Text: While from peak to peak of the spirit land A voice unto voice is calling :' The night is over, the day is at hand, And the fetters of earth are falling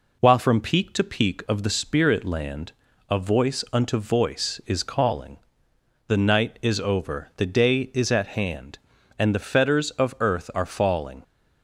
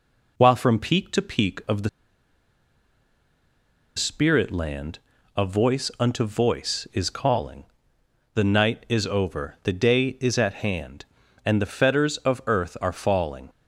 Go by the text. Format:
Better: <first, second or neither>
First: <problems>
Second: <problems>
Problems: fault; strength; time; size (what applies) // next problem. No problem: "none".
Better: first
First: pauses between "land" and "A"; slight; at 2.7 s; 0.36 s long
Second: pauses between "the" and "spirit"; strong; at 1.8 s; 2.0 s long // pauses between "land" and "A"; slight; at 4.9 s; 0.36 s long